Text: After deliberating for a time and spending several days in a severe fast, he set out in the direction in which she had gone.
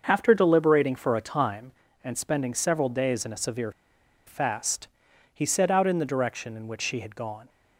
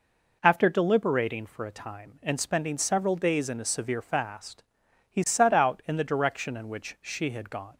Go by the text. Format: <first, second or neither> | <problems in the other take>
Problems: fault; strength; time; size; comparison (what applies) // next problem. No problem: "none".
second | starts louder than the rest; until 1.0 s; 6 dB // pauses between "severe" and "fast"; noticeable; at 3.7 s; 0.55 s long